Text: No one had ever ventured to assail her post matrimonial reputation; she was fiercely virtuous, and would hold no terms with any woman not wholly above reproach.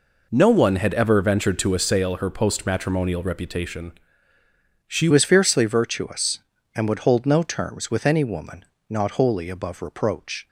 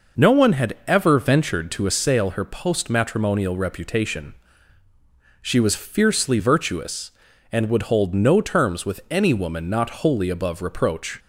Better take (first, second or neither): second